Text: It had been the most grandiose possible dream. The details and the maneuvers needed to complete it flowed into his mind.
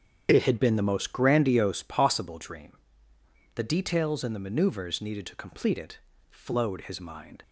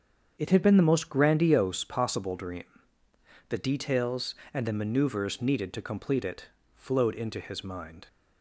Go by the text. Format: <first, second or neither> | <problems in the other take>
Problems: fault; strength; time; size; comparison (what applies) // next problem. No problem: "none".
second | starts louder than the rest; strong; until 1.3 s; 8 dB; strong in the second // pauses between "it" and "flowed"; slight; at 5.9 s; 0.32 s long; slight in the second // skips "into"; at 6.8 s